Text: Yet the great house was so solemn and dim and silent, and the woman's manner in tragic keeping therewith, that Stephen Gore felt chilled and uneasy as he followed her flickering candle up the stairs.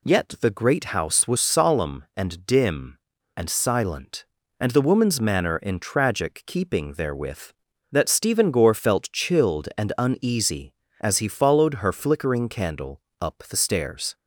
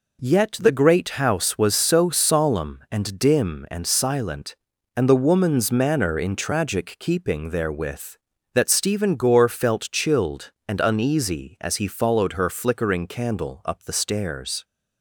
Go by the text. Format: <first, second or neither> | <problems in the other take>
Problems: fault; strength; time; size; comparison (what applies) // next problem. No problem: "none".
second | skips "so"; at 1.3 s // pauses between "candle" and "up"; slight; at 13.0 s; 0.18 s long